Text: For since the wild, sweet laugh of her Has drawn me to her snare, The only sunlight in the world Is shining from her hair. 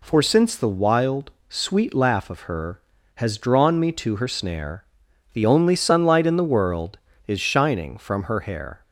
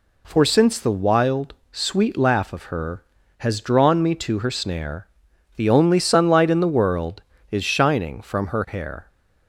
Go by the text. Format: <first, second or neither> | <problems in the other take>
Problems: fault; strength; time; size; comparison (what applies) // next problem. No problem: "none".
neither | none